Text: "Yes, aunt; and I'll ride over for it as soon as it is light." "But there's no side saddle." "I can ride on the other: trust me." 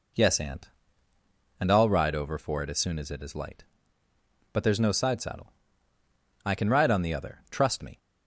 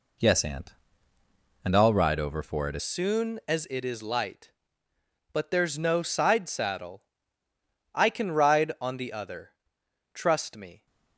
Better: first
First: none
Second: changes voice at "soon"; from 2.8 s on; 8.0 s long

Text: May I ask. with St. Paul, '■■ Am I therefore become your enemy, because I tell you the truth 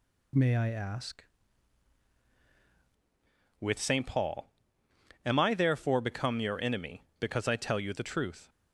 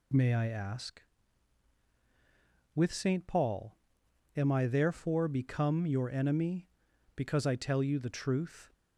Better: second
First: changes voice at "with"; from 3.6 s on; 4.8 s long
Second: none

